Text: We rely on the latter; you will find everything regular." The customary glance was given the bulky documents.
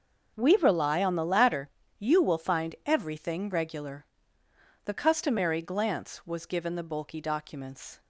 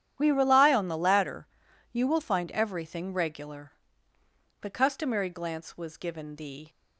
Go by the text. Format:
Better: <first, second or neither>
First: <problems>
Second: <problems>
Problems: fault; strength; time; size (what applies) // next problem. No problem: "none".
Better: first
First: starts louder than the rest; noticeable; until 1.3 s; 6 dB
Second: starts louder than the rest; strong; until 1.2 s; 10 dB // stops before "bulky documents"; at 6.6 s